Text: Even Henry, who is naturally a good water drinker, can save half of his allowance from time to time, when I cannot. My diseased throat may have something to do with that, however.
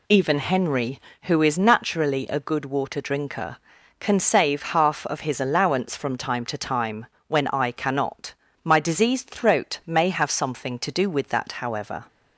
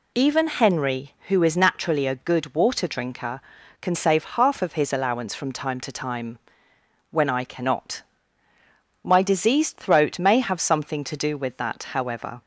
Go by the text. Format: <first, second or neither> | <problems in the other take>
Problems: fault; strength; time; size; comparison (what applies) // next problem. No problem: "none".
neither | none